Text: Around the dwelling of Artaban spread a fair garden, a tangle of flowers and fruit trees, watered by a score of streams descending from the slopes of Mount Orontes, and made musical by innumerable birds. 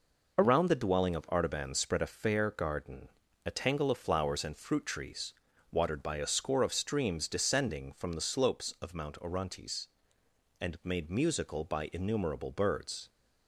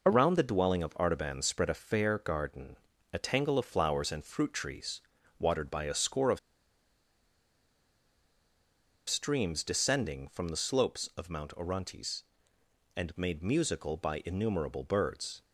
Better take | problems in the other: first | pauses between "of" and "streams"; strong; at 6.3 s; 2.7 s long

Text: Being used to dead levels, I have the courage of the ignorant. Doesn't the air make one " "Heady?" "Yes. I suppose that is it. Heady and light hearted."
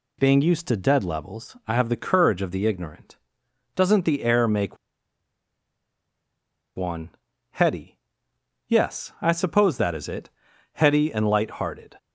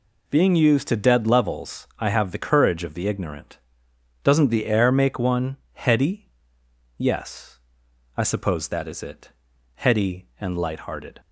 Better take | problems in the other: second | pauses between "make" and "one"; strong; at 4.7 s; 1.9 s long

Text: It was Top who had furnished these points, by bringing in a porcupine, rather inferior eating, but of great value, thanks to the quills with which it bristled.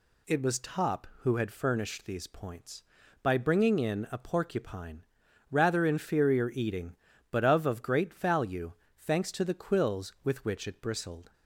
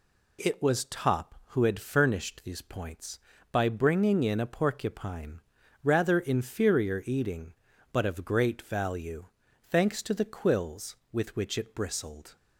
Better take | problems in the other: second | says "of" twice; at 7.6 s

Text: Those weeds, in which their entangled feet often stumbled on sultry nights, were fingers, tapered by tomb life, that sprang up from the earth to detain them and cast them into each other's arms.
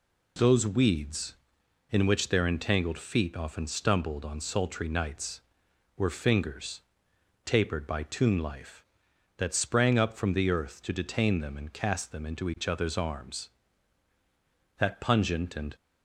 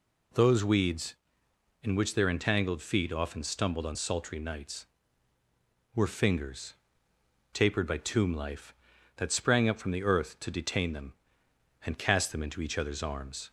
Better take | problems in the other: second | goes on to say "That pungent and"; noticeable; from 14.7 s on; 0.98 s long

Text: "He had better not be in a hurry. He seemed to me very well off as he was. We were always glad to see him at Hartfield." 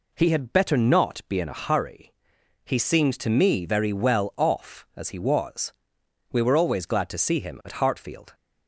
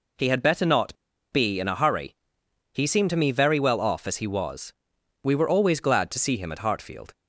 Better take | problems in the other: first | pauses between "not" and "be"; at 0.9 s; 0.37 s long

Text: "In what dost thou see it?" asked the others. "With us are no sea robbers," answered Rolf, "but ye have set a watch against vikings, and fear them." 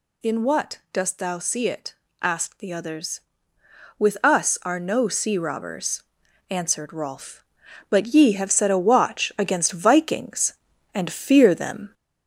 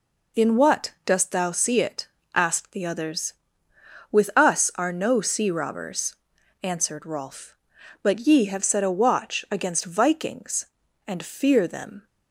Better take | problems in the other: second | gets louder; slight; throughout; 2.5 dB

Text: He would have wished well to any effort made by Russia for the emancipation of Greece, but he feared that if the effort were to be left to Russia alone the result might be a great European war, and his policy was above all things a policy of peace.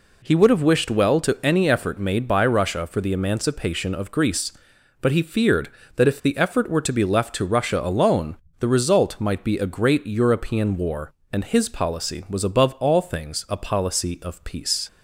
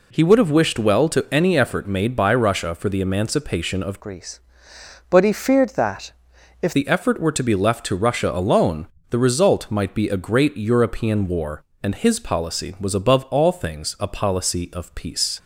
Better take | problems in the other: first | changes voice from "Greece" to "if"; from 4.0 to 6.7 s; 2.7 s long // pauses between "that" and "if"; noticeable; at 6.1 s; 0.50 s long // pauses between "alone" and "the"; slight; at 8.8 s; 0.24 s long; slight in the first

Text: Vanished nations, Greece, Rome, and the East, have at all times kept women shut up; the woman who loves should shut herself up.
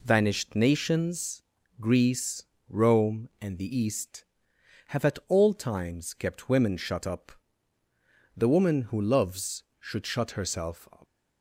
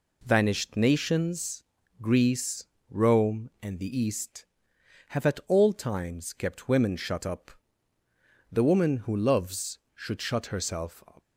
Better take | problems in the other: neither | none

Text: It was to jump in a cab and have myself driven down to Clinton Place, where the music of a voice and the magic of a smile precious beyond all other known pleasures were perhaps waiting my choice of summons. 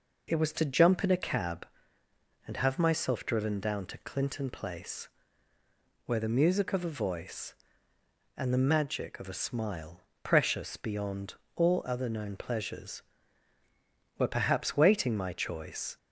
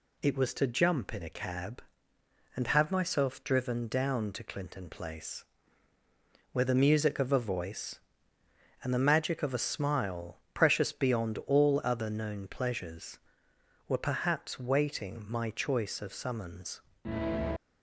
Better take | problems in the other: second | pauses between "smile" and "precious"; slight; at 10.0 s; 0.22 s long; slight in the second // pauses between "beyond" and "all"; slight; at 11.3 s; 0.22 s long // stops before "of summons"; at 15.9 s

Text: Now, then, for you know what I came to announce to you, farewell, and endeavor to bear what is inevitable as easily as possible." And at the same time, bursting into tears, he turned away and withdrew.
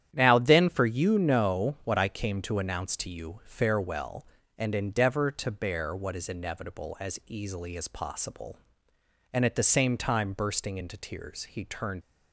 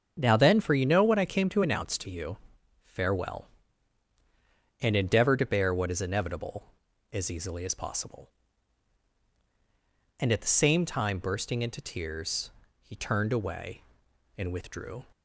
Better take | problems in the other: second | starts louder than the rest; strong; until 1.1 s; 10 dB; strong in the second // stops before "away and withdrew"; at 12.0 s

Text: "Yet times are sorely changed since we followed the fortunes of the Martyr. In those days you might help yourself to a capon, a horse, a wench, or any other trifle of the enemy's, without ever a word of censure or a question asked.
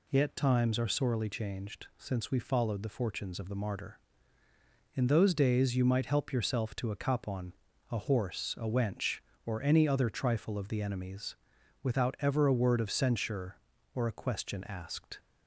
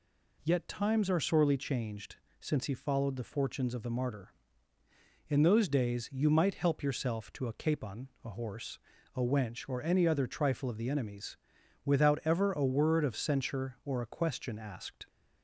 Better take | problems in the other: first | pauses between "changed" and "since"; slight; at 2.1 s; 0.24 s long // says "he" for "we"; at 2.6 s

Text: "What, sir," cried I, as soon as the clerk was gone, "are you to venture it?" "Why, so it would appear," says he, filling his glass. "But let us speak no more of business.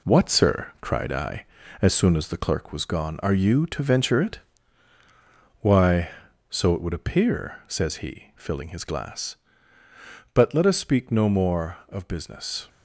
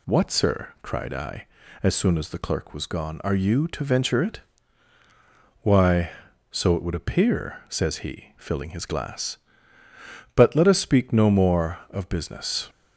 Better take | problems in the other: second | gets quieter; throughout; 6.5 dB

